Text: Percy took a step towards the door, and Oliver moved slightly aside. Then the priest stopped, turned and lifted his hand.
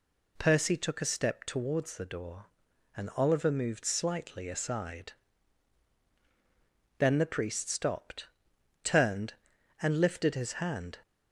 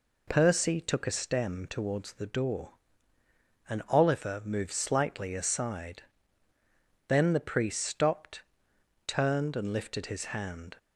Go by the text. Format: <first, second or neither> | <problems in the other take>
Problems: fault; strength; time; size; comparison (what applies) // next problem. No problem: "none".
first | says "stem" for "step"; at 1.1 s